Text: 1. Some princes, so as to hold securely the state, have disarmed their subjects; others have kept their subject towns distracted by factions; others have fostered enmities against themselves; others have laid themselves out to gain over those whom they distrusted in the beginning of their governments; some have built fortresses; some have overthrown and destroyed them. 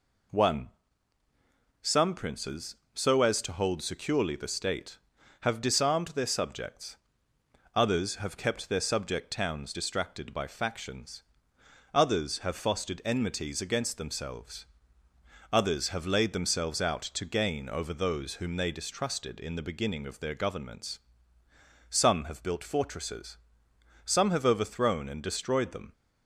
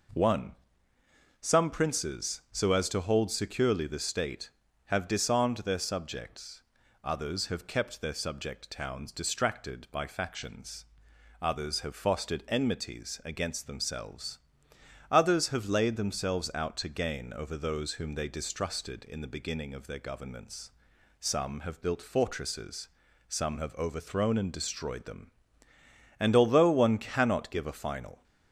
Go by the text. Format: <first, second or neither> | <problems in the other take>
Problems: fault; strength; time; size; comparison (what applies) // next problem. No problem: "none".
first | goes on to say "And although one cannot give a final"; strong; from 26.1 s on; 2.0 s long